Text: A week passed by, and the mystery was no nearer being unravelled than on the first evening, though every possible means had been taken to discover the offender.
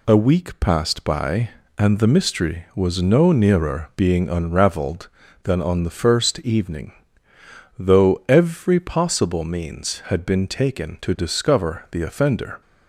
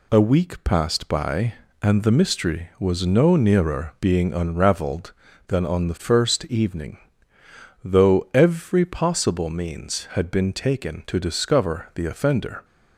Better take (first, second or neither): neither